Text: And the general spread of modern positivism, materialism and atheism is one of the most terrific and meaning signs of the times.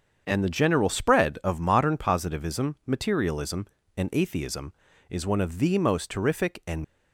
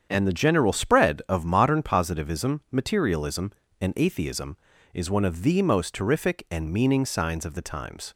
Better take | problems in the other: second | starts louder than the rest; strong; until 1.2 s; 7.5 dB; strong in the second // stops before "meaning signs of the times"; at 6.8 s

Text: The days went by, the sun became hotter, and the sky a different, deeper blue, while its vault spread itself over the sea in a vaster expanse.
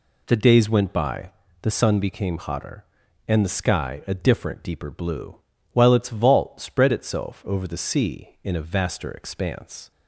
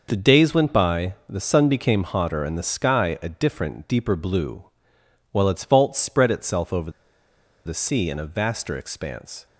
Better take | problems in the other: first | pauses between "over" and "the"; noticeable; at 6.8 s; 0.76 s long

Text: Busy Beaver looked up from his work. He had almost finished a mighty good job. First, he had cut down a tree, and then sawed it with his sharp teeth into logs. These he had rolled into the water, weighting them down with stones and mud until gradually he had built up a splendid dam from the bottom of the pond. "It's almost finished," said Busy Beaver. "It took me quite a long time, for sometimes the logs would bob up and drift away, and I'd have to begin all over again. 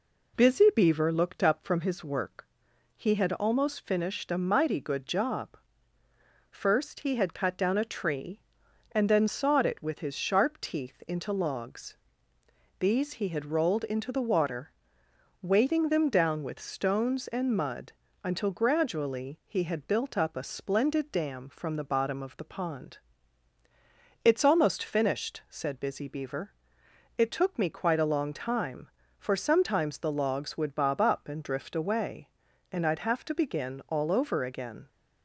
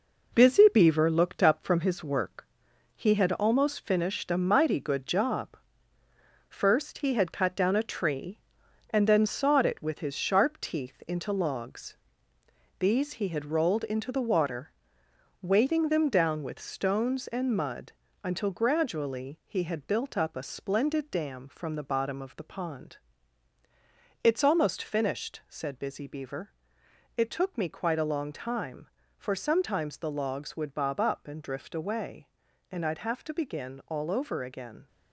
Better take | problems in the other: first | gets quieter; throughout; 6.5 dB // pauses between "mud" and "until"; slight; at 17.9 s; 0.32 s long; slight in the first

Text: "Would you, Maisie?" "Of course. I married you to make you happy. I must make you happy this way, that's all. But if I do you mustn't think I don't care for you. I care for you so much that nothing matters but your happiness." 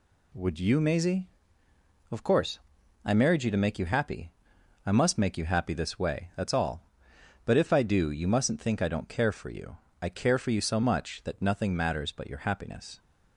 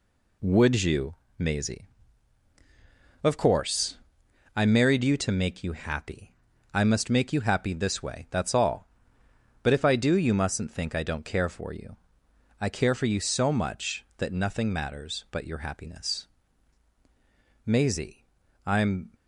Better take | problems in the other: first | goes on to say "Maisie I'm"; from 17.6 s on; 1.4 s long

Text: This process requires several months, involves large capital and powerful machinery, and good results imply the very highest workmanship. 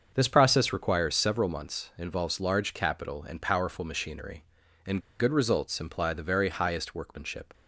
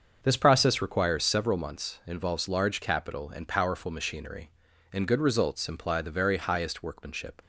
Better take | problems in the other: second | starts louder than the rest; until 1.1 s; 6.5 dB; also in the second // pauses between "and" and "good"; slight; at 5.0 s; 0.18 s long

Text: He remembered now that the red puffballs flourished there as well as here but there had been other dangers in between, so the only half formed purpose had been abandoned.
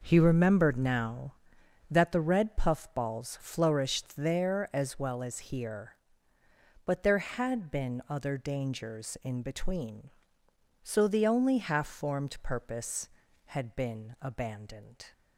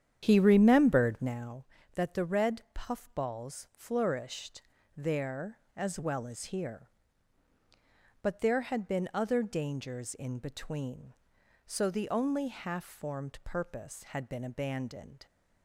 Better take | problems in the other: first | starts louder than the rest; strong; until 1.4 s; 9 dB // pauses between "flourished" and "there"; slight; at 4.6 s; 0.34 s long

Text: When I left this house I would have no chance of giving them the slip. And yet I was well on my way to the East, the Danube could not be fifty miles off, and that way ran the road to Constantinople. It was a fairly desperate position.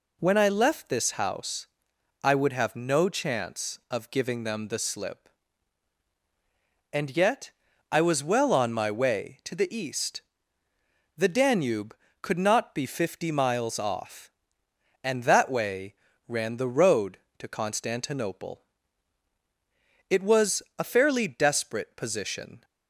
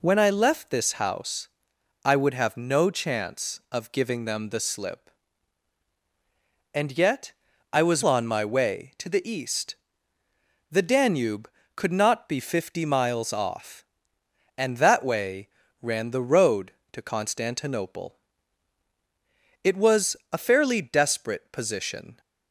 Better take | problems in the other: first | pauses between "house" and "I"; noticeable; at 1.4 s; 0.56 s long; noticeable in the first // pauses between "yet" and "I"; at 7.3 s; 0.38 s long; also in the first // skips "well"; at 8.0 s // pauses between "way" and "ran"; slight; at 15.4 s; 0.34 s long; slight in the first // pauses between "was" and "a"; slight; at 20.1 s; 0.16 s long; slight in the first

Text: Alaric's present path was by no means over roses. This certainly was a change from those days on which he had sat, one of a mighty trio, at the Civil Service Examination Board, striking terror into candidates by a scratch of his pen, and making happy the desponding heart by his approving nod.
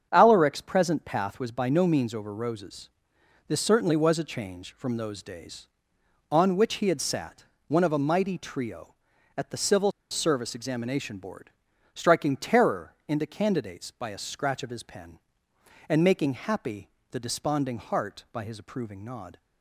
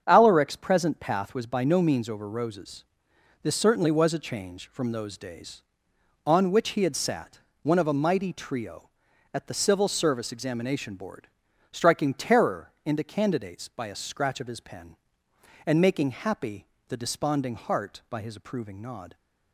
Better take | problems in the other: second | starts louder than the rest; strong; until 1.1 s; 7.5 dB; strong in the second // pauses between "Civil" and "Service"; slight; at 9.9 s; 0.19 s long // pauses between "terror" and "into"; slight; at 12.9 s; 0.16 s long; slight in the second // pauses between "happy" and "the"; slight; at 16.8 s; 0.22 s long; slight in the second

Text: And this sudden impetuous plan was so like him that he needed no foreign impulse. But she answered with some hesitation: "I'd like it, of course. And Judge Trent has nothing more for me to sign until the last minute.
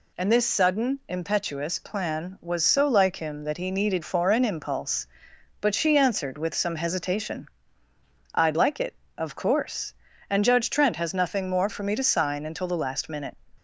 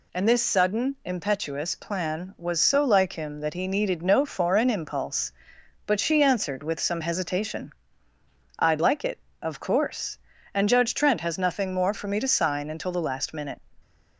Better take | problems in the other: second | skips "no"; at 4.0 s

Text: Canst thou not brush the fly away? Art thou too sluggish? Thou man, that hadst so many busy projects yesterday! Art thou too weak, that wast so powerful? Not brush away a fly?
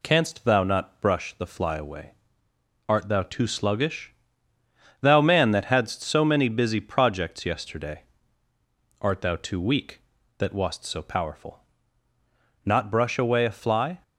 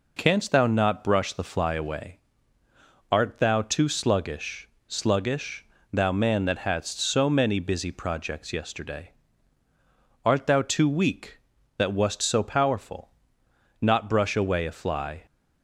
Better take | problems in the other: first | says "sluggish" twice; at 4.8 s

